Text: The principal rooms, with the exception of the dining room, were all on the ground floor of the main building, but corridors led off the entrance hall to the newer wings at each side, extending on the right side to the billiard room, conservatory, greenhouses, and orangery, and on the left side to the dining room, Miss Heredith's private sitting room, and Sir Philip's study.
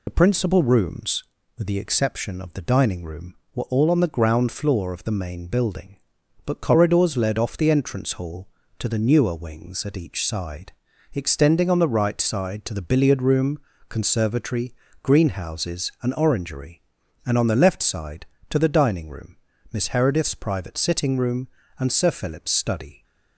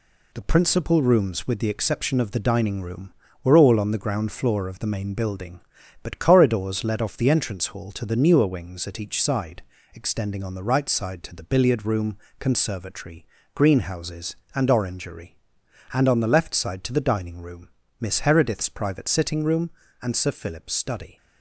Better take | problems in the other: second | loses the start of "The"; at 0.0 s; 60 ms

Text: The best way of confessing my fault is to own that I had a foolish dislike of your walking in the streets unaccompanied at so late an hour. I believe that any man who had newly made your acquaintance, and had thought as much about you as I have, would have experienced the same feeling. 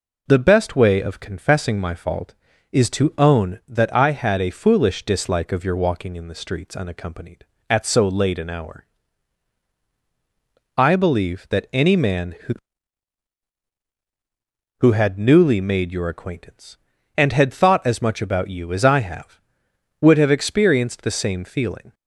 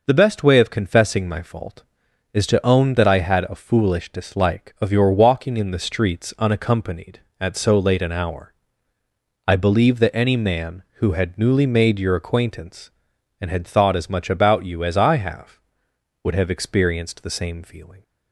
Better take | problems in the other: second | says "who" twice; at 14.7 s

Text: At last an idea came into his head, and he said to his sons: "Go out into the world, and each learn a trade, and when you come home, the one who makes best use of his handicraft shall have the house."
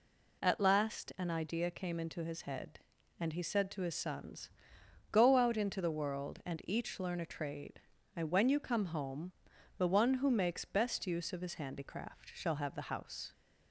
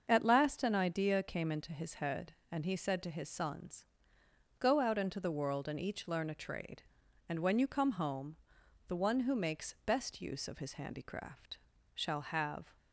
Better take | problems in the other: first | starts louder than the rest; until 1.0 s; 6.5 dB // pauses between "handicraft" and "shall"; slight; at 11.5 s; 0.34 s long // stops before "the house"; at 12.7 s

